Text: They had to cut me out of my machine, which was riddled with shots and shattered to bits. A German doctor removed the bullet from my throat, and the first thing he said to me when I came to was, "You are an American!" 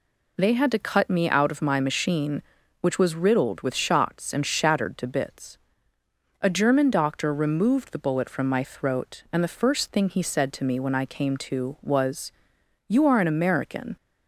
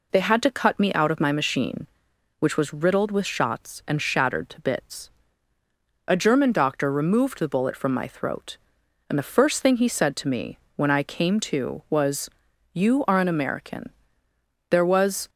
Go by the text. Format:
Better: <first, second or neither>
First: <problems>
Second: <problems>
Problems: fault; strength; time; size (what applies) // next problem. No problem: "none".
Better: first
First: none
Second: pauses between "me" and "when"; slight; at 10.5 s; 0.18 s long // goes on to say "There was"; from 14.6 s on; 0.60 s long